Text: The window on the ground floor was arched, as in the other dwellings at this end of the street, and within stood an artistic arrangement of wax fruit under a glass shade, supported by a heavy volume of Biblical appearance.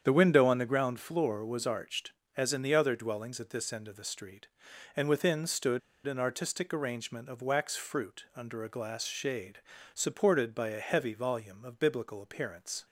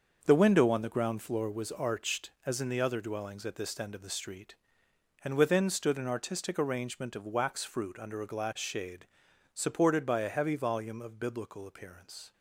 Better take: second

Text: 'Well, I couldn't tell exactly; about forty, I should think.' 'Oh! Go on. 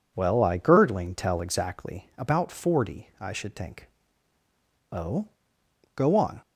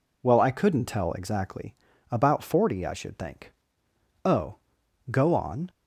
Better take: second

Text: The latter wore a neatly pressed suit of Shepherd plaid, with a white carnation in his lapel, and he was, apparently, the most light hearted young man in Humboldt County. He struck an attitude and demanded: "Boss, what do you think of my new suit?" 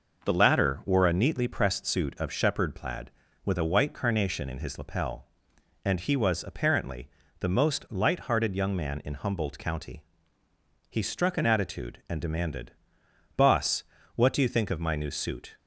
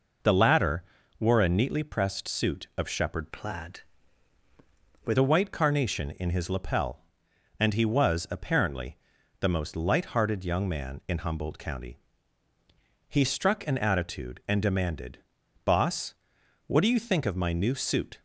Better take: first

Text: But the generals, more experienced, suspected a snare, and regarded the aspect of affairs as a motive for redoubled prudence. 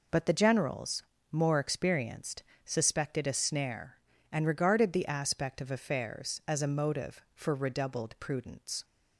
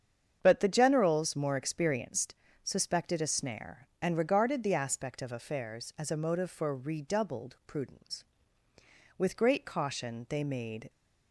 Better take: first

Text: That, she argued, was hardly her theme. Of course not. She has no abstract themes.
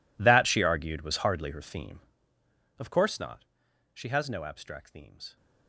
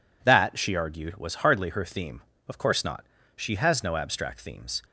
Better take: second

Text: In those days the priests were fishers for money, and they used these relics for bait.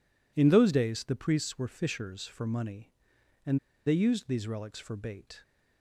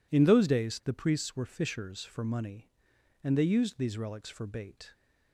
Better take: second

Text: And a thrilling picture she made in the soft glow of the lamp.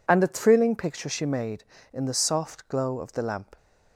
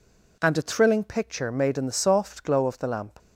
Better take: first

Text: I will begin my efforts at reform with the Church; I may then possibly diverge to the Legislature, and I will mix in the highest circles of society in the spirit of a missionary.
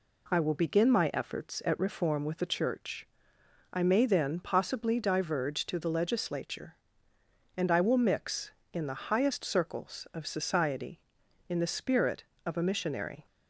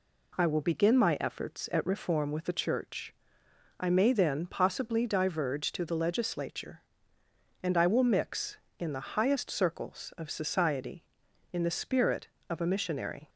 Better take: neither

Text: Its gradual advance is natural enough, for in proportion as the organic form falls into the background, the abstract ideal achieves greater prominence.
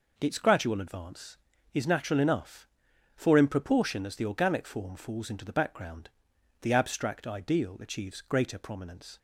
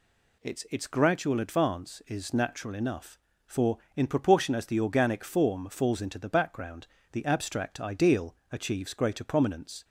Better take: first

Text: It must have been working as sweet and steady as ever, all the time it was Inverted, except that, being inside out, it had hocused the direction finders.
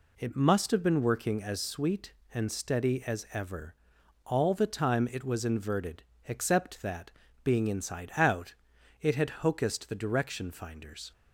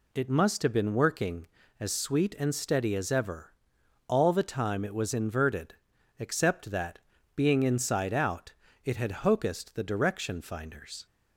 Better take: neither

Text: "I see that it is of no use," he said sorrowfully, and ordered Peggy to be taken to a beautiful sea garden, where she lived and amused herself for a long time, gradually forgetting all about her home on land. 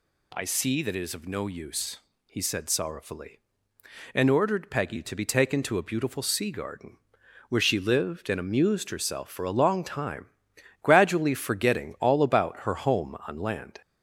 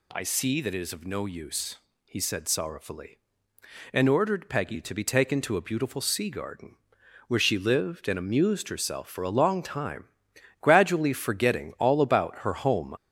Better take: first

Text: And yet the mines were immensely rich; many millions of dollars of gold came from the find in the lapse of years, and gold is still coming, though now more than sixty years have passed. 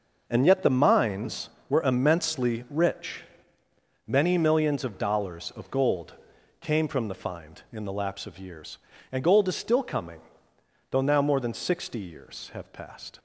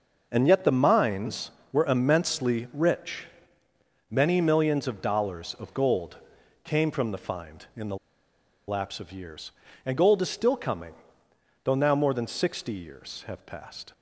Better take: first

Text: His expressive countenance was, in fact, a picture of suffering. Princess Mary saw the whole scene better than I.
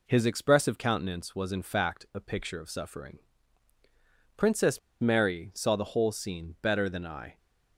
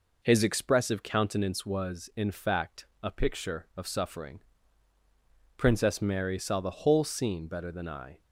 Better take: second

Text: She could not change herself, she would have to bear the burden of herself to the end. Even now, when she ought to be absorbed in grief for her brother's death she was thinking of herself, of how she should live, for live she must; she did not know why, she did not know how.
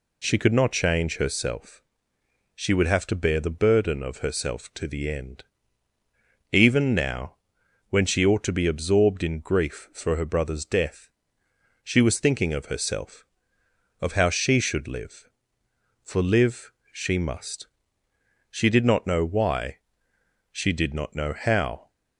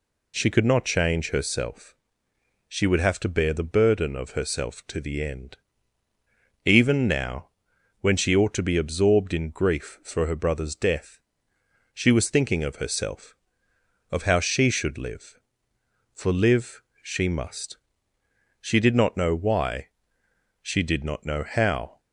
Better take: neither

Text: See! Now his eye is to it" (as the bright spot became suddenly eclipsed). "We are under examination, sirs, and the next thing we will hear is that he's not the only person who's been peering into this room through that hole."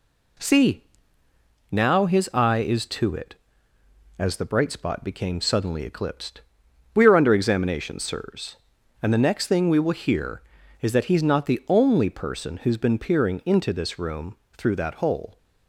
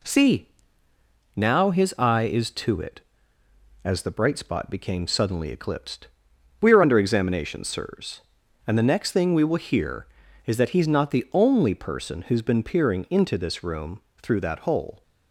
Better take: neither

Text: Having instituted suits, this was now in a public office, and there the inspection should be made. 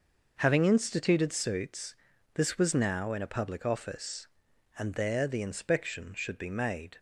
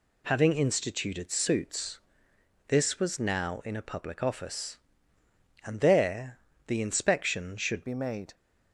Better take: first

